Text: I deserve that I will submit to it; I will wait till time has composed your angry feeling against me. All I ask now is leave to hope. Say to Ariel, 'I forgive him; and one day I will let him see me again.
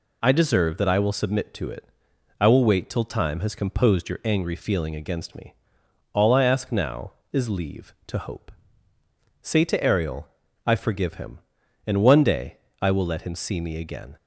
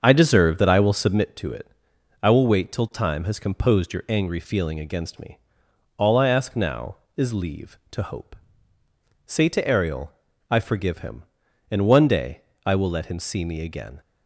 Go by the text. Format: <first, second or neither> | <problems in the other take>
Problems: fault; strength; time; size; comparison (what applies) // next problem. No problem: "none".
first | starts louder than the rest; until 1.3 s; 7 dB // pauses between "day" and "I"; slight; at 12.4 s; 0.26 s long; slight in the first